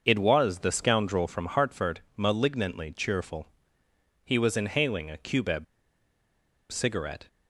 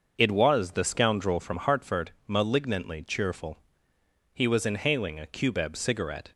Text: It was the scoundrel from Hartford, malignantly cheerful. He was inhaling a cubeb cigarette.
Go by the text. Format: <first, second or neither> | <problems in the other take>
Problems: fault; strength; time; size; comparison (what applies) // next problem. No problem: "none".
second | starts louder than the rest; until 1.0 s; 6.5 dB; also in the second // pauses between "cubeb" and "cigarette"; at 5.6 s; 1.0 s long